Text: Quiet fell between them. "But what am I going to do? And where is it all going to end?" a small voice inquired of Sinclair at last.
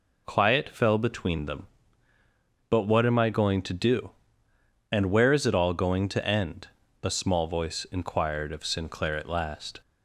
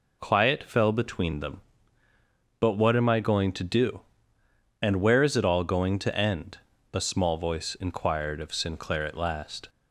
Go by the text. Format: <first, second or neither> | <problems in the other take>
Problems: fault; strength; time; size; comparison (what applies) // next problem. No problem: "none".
neither | none